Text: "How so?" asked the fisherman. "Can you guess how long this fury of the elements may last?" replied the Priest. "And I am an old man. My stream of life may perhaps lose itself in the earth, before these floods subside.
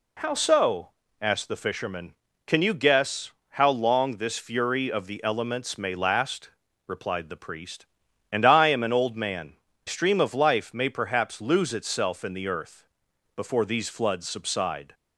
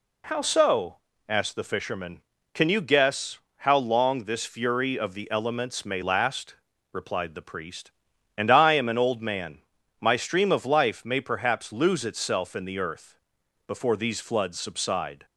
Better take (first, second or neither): second